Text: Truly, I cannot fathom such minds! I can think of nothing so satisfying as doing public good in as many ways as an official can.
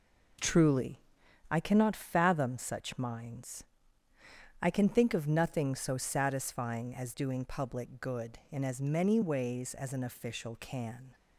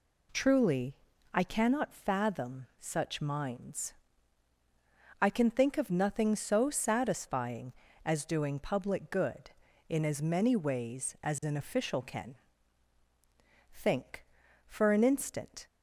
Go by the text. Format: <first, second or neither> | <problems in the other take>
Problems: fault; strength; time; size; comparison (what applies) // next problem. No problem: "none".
first | goes on to say "Think for an instant"; strong; from 13.7 s on; 1.9 s long